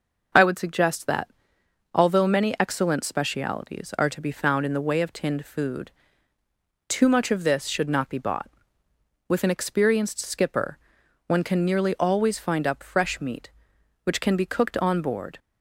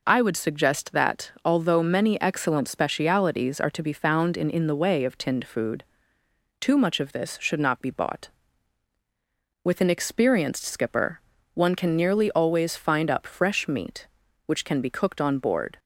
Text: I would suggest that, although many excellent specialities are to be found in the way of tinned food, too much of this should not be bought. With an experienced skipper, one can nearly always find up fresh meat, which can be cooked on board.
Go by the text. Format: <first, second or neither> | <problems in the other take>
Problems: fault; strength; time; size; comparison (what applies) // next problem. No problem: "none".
first | says "in" twice; at 4.5 s